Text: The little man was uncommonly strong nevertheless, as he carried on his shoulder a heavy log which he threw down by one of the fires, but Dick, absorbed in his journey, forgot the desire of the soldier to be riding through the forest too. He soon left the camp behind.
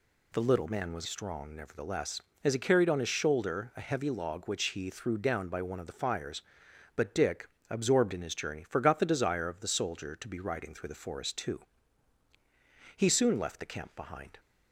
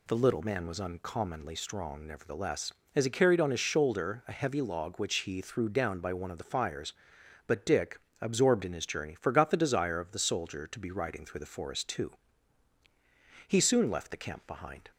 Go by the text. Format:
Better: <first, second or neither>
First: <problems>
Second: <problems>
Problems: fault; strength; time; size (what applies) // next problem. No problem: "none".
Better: second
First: skips "uncommonly"; at 1.0 s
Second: none